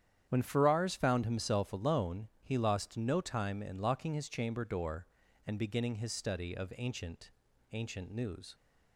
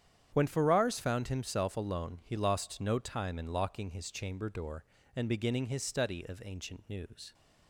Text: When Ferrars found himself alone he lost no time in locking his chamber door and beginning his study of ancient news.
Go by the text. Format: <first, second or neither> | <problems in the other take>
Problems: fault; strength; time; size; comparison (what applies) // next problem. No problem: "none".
second | starts louder than the rest; strong; until 1.2 s; 9.5 dB; strong in the second // says "ancient" twice; at 7.7 s